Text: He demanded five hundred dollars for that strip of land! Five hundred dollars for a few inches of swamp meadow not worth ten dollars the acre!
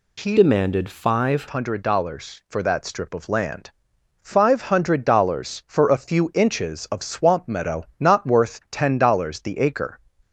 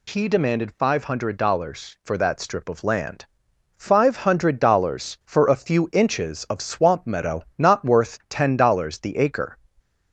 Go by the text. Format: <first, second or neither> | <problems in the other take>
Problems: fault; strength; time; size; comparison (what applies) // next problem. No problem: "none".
second | changes voice from "demanded" to "five"; from 0.3 to 1.4 s; 1.1 s long